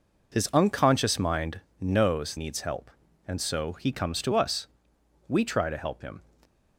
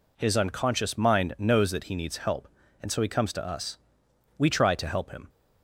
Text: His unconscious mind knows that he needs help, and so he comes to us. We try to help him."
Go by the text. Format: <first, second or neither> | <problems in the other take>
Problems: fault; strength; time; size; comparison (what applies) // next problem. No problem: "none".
second | pauses between "mind" and "knows"; slight; at 1.6 s; 0.18 s long // skips "that he"; at 2.3 s